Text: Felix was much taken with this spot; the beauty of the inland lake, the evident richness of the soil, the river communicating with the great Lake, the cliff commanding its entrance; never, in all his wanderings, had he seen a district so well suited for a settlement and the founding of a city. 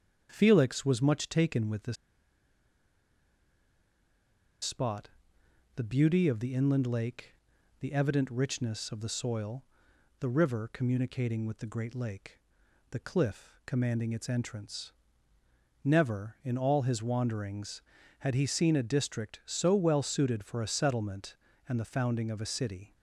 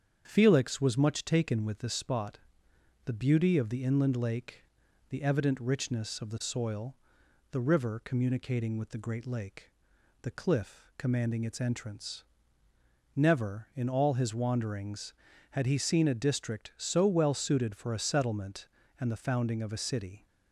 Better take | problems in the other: second | starts louder than the rest; strong; until 1.3 s; 7.5 dB; strong in the second // pauses between "this" and "spot"; strong; at 1.9 s; 2.6 s long

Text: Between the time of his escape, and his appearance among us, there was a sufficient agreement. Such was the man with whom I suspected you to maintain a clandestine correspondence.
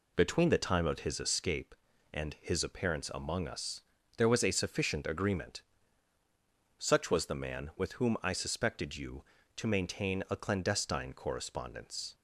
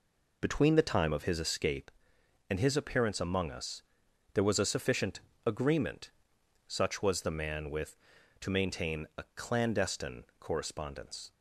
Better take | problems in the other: first | pauses between "sufficient" and "agreement"; slight; at 5.1 s; 0.26 s long // skips "whom I suspected you"; at 8.1 s

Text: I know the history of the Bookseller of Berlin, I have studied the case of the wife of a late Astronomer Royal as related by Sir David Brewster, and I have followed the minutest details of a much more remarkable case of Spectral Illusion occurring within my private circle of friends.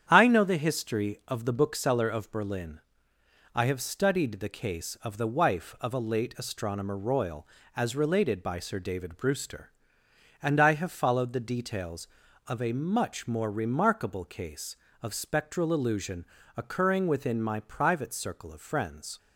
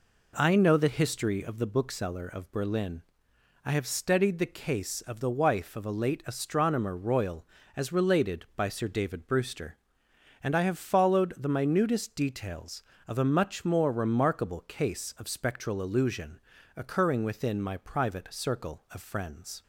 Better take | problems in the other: second | starts louder than the rest; strong; until 1.1 s; 9 dB // skips "minutest"; at 11.3 s // pauses between "Illusion" and "occurring"; slight; at 16.2 s; 0.32 s long; slight in the second

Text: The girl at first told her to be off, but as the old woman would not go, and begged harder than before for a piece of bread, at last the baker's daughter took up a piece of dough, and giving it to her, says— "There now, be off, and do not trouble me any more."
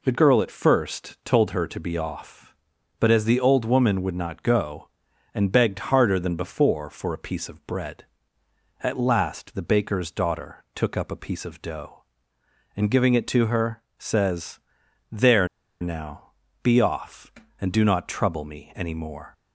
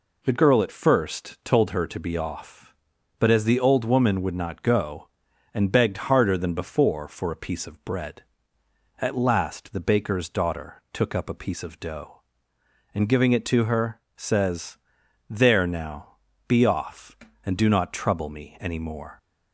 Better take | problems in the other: second | pauses between "There" and "now"; slight; at 15.4 s; 0.33 s long

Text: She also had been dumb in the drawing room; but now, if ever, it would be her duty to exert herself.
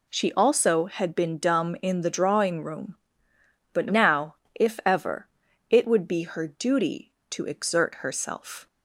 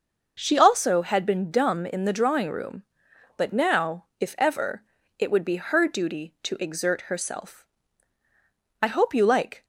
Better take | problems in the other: first | goes on to say "I hope you like"; noticeable; from 8.8 s on; 0.84 s long

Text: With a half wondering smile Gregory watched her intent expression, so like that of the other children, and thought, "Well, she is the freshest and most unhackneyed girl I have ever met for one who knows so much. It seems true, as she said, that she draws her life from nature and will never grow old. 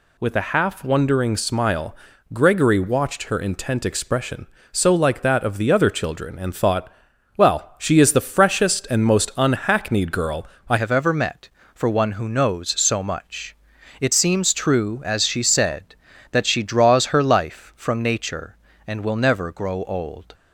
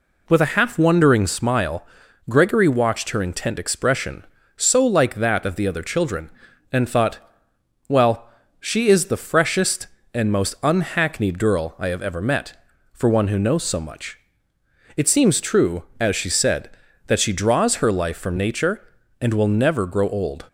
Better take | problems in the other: second | pauses between "smile" and "Gregory"; at 1.9 s; 0.38 s long; also in the second // pauses between "girl" and "I"; slight; at 10.4 s; 0.22 s long // changes voice at "have"; from 10.7 s on; 9.6 s long

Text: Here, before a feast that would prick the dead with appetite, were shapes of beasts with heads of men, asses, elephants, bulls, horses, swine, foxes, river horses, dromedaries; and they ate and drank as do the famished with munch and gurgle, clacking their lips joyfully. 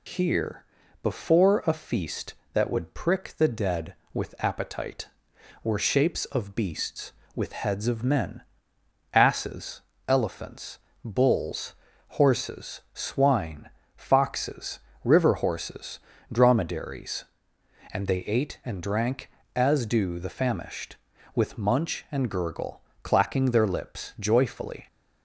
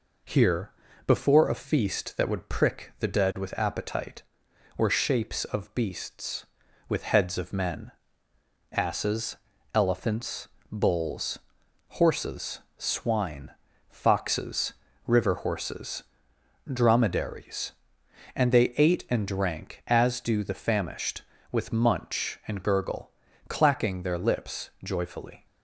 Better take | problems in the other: neither | none

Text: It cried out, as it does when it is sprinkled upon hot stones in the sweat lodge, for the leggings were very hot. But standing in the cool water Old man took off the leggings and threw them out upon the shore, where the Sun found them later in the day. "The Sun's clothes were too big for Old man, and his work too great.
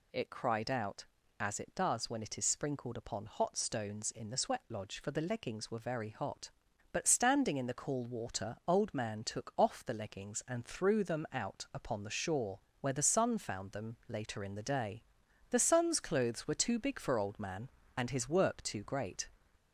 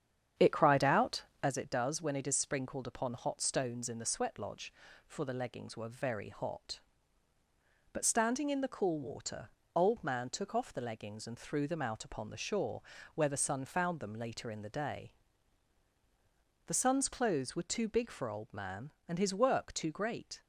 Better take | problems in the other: first | starts louder than the rest; strong; until 1.5 s; 8.5 dB // pauses between "water" and "Old"; slight; at 9.5 s; 0.26 s long

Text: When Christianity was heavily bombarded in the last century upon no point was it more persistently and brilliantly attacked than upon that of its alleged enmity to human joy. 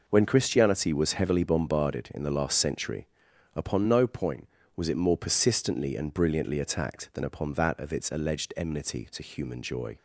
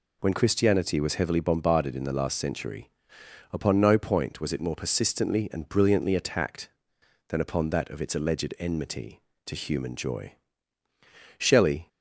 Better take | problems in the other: first | pauses between "century" and "upon"; noticeable; at 2.8 s; 0.60 s long; noticeable in the first // goes on to say "Shelley"; from 11.3 s on; 0.50 s long

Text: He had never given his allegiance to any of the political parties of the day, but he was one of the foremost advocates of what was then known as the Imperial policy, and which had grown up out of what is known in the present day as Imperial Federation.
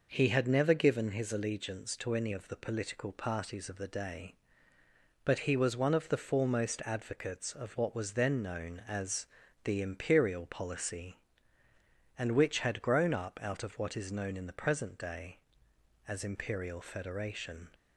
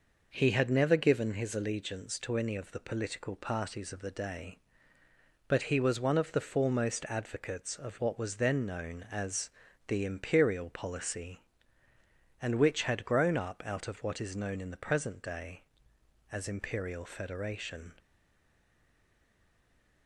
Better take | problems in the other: first | pauses between "as" and "the"; at 9.5 s; 0.38 s long; also in the first // stays silent after the last word; noticeable; from 17.9 s on; 2.1 s long

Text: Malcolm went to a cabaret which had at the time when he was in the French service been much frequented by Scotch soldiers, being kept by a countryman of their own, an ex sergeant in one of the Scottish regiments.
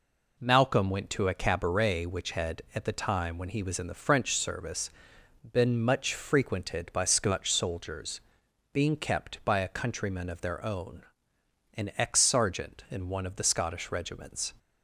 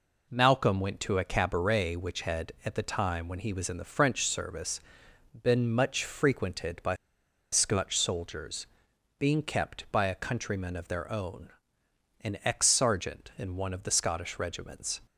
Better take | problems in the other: first | pauses between "service" and "been"; noticeable; at 4.7 s; 0.64 s long; noticeable in the first // pauses between "by" and "Scotch"; noticeable; at 6.9 s; 0.58 s long

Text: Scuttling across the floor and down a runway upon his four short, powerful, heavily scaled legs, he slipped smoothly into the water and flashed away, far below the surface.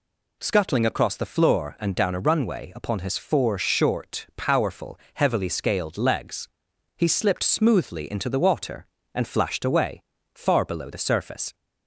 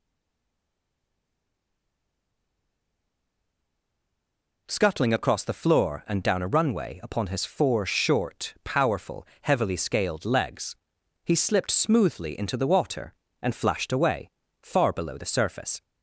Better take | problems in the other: first | stays silent before the first word; strong; until 4.6 s; 4.6 s long

